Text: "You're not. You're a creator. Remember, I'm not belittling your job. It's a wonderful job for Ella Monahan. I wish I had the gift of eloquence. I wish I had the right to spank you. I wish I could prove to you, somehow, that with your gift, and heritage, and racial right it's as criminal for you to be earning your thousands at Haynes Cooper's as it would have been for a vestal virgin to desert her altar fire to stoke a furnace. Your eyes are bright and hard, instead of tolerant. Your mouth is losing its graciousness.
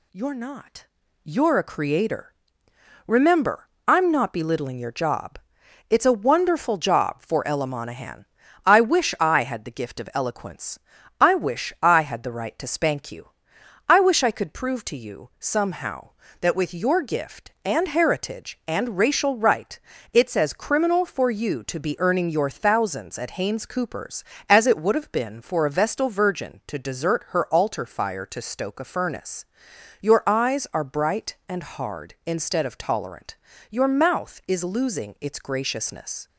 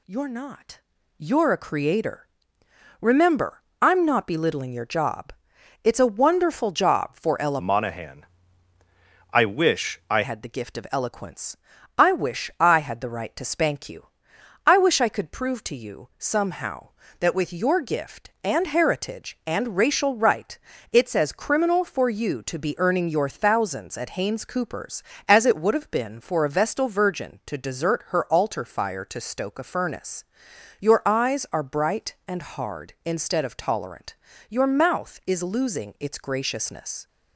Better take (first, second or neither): first